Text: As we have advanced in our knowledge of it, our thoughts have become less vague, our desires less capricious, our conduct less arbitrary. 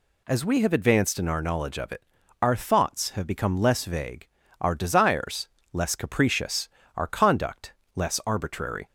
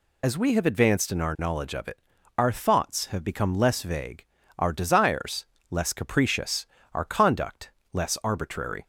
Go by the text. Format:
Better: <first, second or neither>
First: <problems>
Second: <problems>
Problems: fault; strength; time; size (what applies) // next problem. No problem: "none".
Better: first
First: pauses between "desires" and "less"; slight; at 5.4 s; 0.24 s long // pauses between "conduct" and "less"; slight; at 7.7 s; 0.24 s long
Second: loses the start of "As"; at 0.2 s; 50 ms // pauses between "desires" and "less"; slight; at 5.4 s; 0.24 s long // pauses between "conduct" and "less"; slight; at 7.6 s; 0.24 s long